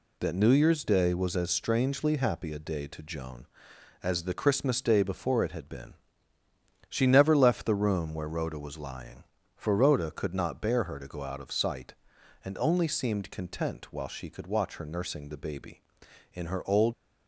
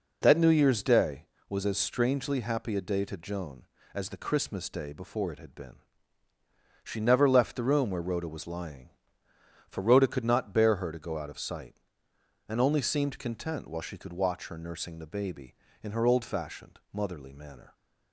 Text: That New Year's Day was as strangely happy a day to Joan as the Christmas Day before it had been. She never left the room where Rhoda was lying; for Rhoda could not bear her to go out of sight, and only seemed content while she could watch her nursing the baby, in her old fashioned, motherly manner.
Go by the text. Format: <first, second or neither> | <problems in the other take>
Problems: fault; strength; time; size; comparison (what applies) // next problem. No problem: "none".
second | stops before "fashioned motherly manner"; at 16.9 s